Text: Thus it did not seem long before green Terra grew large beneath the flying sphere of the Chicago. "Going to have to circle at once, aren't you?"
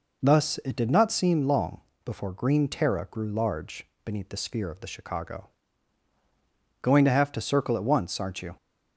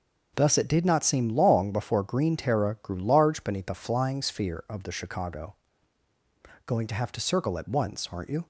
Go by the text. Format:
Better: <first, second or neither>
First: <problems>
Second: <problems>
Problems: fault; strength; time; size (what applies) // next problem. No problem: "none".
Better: second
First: pauses between "long" and "before"; slight; at 1.8 s; 0.24 s long // pauses between "large" and "beneath"; slight; at 3.8 s; 0.18 s long // skips "flying"; at 4.3 s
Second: none